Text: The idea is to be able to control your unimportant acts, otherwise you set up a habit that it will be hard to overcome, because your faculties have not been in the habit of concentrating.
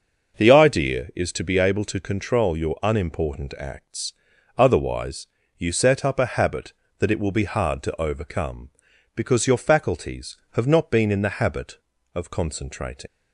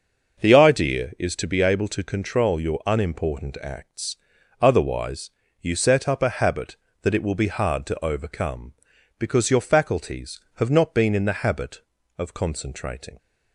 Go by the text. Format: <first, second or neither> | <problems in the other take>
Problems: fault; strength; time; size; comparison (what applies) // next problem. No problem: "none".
second | starts louder than the rest; noticeable; until 1.3 s; 6 dB // pauses between "otherwise" and "you"; slight; at 5.2 s; 0.30 s long; slight in the second // leaves "concentrating" unfinished; at 13.0 s; 65 ms